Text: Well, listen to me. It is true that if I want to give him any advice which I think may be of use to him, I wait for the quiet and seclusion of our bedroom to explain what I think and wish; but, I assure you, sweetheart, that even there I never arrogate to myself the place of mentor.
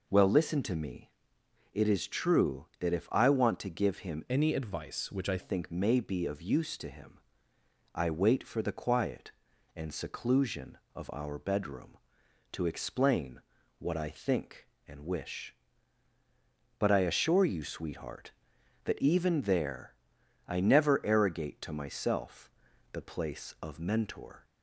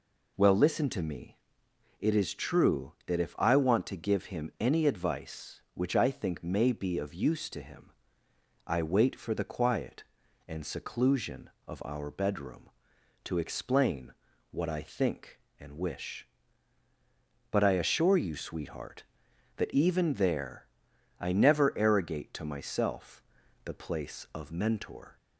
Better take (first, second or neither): second